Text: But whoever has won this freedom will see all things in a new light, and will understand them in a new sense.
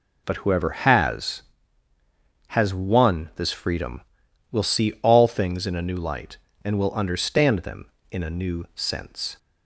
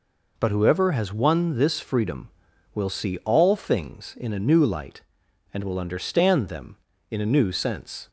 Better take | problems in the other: second | says "has" twice; at 2.4 s

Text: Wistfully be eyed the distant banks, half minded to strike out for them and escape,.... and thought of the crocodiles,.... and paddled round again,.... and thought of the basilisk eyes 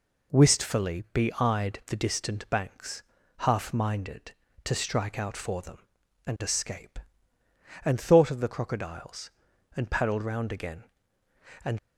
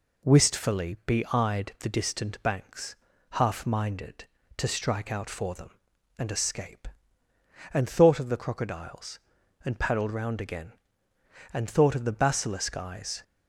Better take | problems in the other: second | stops before "thought of the basilisk eyes"; at 11.7 s

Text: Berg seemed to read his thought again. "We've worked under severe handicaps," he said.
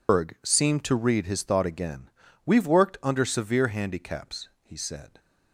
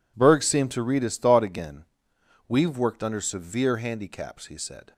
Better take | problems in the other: second | loses the start of "Berg"; at 0.0 s; 155 ms

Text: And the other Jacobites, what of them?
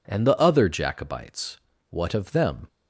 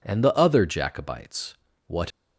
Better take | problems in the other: first | stops before "of them"; at 2.1 s

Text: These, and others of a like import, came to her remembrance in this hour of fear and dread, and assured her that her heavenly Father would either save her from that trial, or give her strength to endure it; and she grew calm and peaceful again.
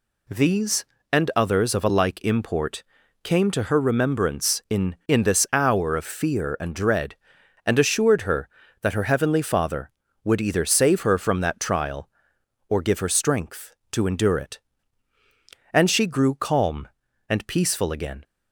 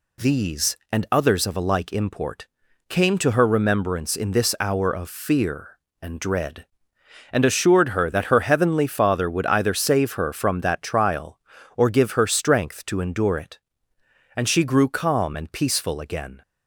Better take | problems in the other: second | says "in" twice; at 5.0 s

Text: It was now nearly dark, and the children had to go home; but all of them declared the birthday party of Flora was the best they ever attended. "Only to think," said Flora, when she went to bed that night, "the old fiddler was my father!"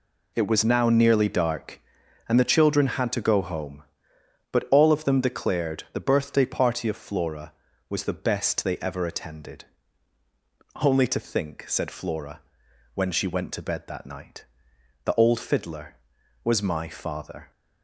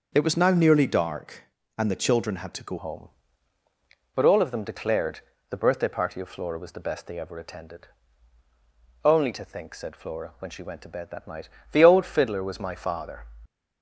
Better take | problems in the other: first | starts louder than the rest; noticeable; until 1.1 s; 6 dB // changes voice at "home"; from 2.7 s on; 10.5 s long // pauses between "declared" and "the"; slight; at 5.1 s; 0.30 s long

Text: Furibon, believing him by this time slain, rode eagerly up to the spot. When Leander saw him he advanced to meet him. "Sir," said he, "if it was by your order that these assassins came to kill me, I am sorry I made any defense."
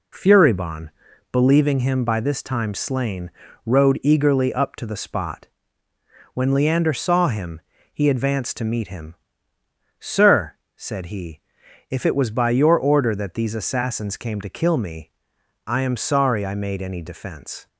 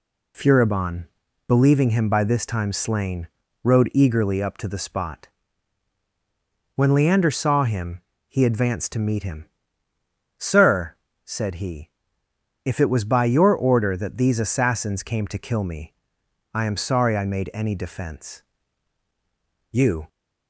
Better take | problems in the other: first | pauses between "him" and "he"; slight; at 8.0 s; 0.26 s long; slight in the first // goes on to say "You"; slight; from 19.7 s on; 0.36 s long

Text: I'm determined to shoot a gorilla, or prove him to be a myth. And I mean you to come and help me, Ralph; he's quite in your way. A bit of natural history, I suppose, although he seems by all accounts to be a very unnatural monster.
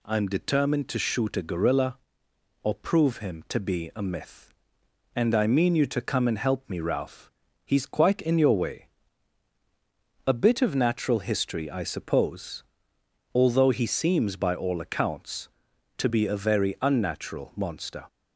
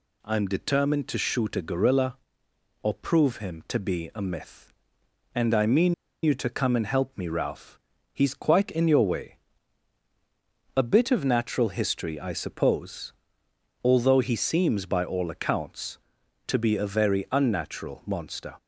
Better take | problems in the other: first | pauses between "mean" and "you"; slight; at 5.9 s; 0.29 s long

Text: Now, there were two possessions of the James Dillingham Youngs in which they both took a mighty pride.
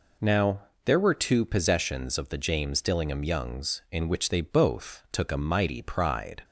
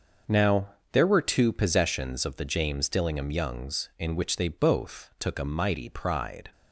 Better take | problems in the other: first | gets quieter; strong; throughout; 10.5 dB

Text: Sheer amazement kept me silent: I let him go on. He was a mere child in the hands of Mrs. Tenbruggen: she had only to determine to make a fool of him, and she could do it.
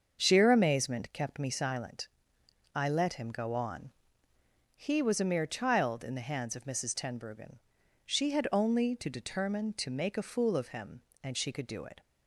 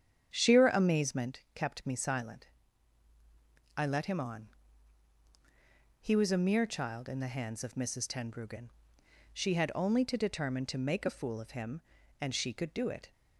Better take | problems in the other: first | starts louder than the rest; strong; until 1.3 s; 8.5 dB; also in the first // skips "go"; at 4.1 s

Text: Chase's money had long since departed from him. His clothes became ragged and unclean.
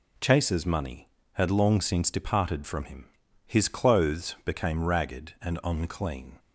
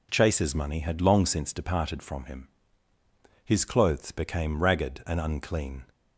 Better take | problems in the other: neither | none

